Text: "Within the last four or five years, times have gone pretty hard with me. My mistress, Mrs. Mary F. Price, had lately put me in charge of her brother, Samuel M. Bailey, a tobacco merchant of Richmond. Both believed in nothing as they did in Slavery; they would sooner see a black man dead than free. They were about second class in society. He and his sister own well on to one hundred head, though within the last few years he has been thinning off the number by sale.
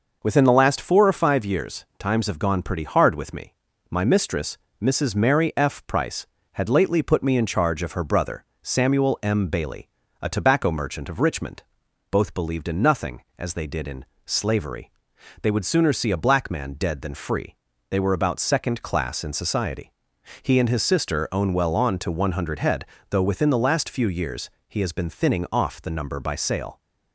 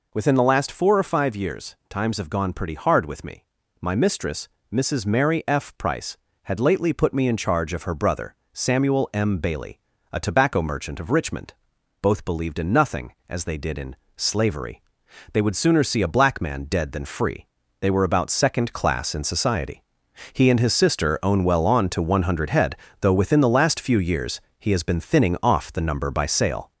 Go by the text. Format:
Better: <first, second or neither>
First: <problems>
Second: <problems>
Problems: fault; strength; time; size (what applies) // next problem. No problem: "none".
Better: first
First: pauses between "in" and "Slavery"; slight; at 14.0 s; 0.22 s long // pauses between "years" and "he"; slight; at 24.4 s; 0.18 s long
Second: gets louder; slight; throughout; 3.5 dB // pauses between "in" and "Slavery"; slight; at 13.9 s; 0.22 s long // pauses between "years" and "he"; slight; at 24.4 s; 0.18 s long